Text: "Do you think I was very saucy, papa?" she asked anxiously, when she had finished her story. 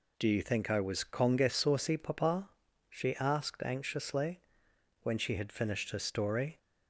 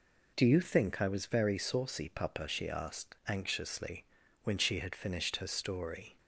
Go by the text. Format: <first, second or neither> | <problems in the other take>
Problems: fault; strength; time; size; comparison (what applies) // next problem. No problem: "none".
second | says "conge" for "very"; at 1.0 s